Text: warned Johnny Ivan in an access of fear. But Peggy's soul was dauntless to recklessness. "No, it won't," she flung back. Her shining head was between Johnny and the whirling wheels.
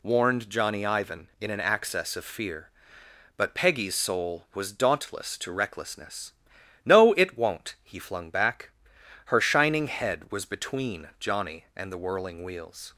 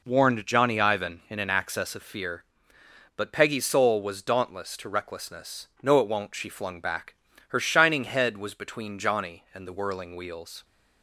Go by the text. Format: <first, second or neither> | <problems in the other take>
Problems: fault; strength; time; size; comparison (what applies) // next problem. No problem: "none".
second | says "he" for "she"; at 7.8 s